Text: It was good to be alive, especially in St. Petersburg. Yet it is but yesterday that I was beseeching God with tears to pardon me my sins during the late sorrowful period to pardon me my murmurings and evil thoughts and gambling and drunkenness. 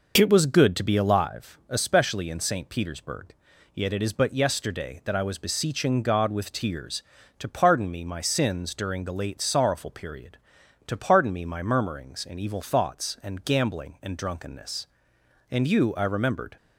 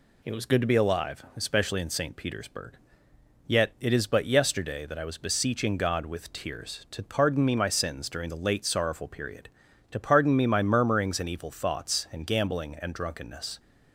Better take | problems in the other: second | goes on to say "And you I remembered"; noticeable; from 15.5 s on; 1.0 s long

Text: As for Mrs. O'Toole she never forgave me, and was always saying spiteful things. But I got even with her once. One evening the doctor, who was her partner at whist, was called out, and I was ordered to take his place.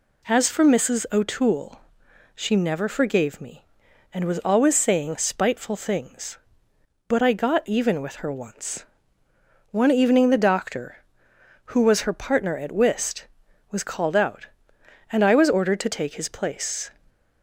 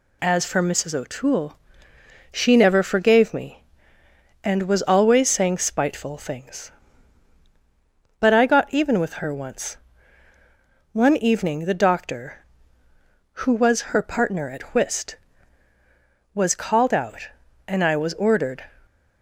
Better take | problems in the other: first | pauses between "O'Toole" and "she"; noticeable; at 1.5 s; 0.74 s long; noticeable in the first // stops before "to take his place"; at 18.8 s

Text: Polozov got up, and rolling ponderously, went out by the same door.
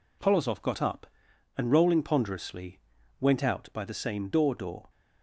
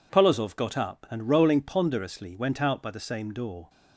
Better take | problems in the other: second | says "door" twice; at 4.5 s

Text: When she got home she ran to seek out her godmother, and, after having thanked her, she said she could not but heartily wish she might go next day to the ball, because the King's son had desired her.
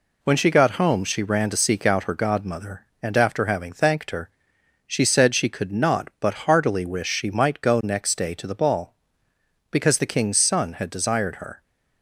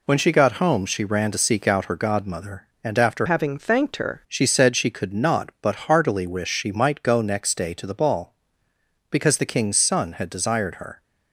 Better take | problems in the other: first | changes voice from "having" to "her"; from 3.2 to 4.2 s; 1.0 s long

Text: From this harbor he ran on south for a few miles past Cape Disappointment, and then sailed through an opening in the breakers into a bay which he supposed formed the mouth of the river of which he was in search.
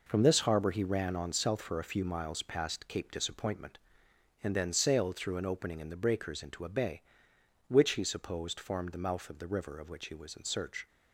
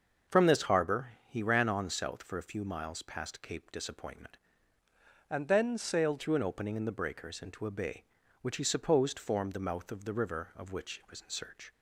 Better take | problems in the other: first | starts louder than the rest; until 1.4 s; 6.5 dB // pauses between "harbor" and "he"; slight; at 1.1 s; 0.16 s long // changes voice from "and" to "sailed"; from 5.2 to 6.1 s; 0.9 s long

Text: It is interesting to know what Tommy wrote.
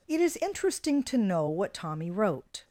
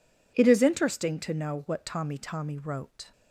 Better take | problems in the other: first | says "Tommy" twice; at 2.1 s

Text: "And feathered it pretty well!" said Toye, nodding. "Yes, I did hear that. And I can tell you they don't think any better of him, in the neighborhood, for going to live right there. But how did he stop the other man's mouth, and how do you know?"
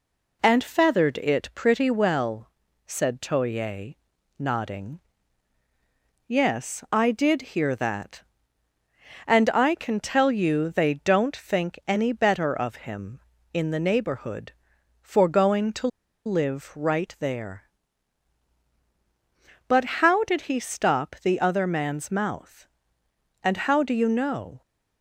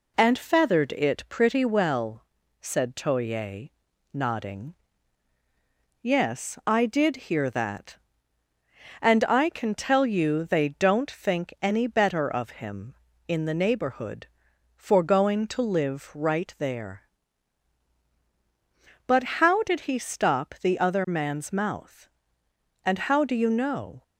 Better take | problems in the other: second | pauses between "to" and "live"; at 15.8 s; 0.38 s long

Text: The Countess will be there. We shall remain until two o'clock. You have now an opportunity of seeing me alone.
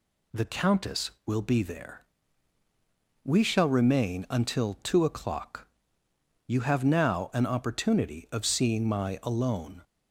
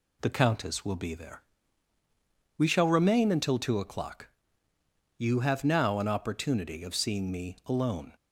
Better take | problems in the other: second | says "my" for "me"; at 8.8 s

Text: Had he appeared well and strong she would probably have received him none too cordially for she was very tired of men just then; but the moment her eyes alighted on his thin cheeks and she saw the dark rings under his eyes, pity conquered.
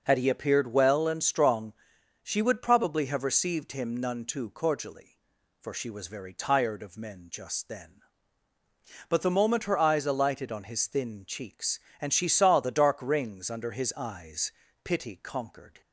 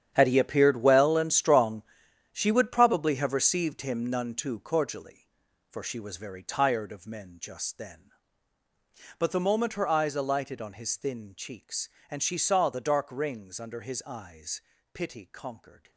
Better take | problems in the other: first | gets quieter; strong; throughout; 14.5 dB // pauses between "strong" and "she"; noticeable; at 1.8 s; 0.50 s long; noticeable in the first

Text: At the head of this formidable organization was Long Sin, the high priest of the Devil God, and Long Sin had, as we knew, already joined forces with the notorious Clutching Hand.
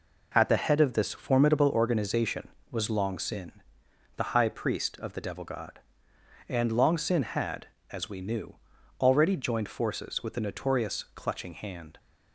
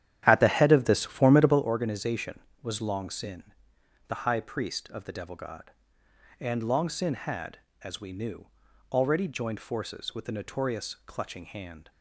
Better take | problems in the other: first | starts louder than the rest; strong; until 1.6 s; 11 dB

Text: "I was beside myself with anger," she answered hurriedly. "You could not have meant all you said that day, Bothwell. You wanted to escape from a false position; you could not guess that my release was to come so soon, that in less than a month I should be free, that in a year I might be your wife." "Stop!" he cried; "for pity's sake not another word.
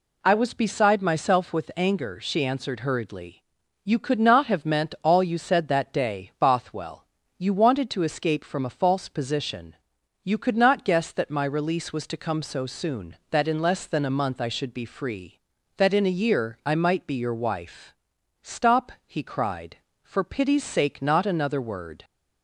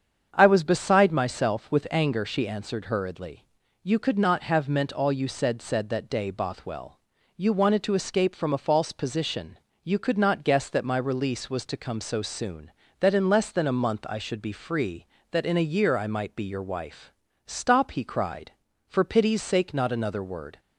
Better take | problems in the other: first | starts louder than the rest; strong; until 1.3 s; 7.5 dB // says "said" twice; at 5.6 s

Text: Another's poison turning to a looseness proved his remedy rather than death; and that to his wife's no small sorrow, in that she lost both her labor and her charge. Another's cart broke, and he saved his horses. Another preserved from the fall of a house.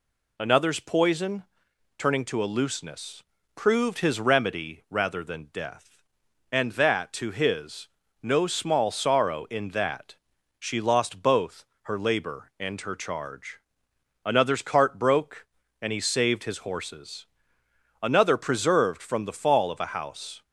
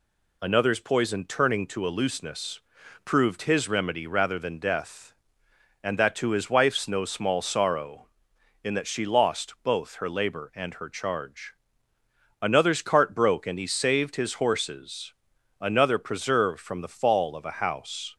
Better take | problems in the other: second | pauses between "poison" and "turning"; noticeable; at 1.4 s; 0.52 s long // pauses between "looseness" and "proved"; slight; at 3.2 s; 0.32 s long; also in the second // skips "wife's"; at 8.0 s // pauses between "that" and "she"; at 10.1 s; 0.42 s long // pauses between "both" and "her"; slight; at 11.6 s; 0.20 s long

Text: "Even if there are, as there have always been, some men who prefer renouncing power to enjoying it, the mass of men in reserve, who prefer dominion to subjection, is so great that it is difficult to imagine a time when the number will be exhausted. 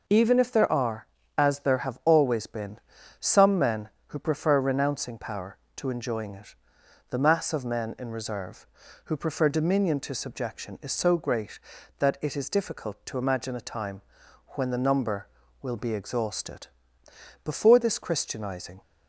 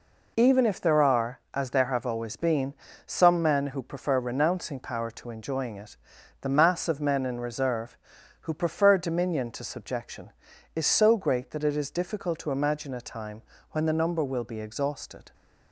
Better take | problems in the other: second | pauses between "time" and "when"; noticeable; at 14.0 s; 0.48 s long; slight in the second // goes on to say "Before this Christianizing"; from 17.4 s on; 1.3 s long

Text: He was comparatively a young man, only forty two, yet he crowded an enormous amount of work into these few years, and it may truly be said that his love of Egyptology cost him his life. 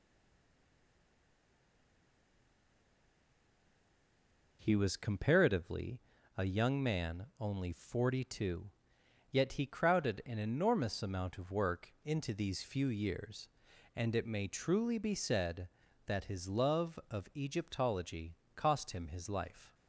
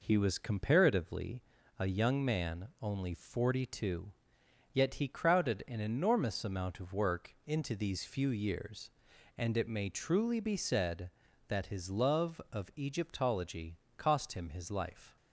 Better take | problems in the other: second | stays silent before the first word; strong; until 4.6 s; 4.6 s long // pauses between "comparatively" and "a"; slight; at 6.0 s; 0.34 s long; slight in the second // pauses between "Egyptology" and "cost"; slight; at 18.3 s; 0.18 s long; slight in the second

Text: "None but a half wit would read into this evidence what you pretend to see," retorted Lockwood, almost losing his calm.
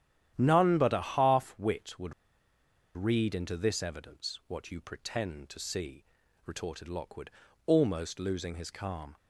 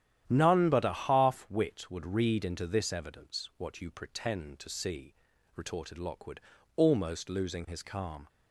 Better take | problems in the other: second | starts louder than the rest; strong; until 1.3 s; 11 dB; strong in the second // pauses between "would" and "read"; noticeable; at 2.1 s; 0.82 s long

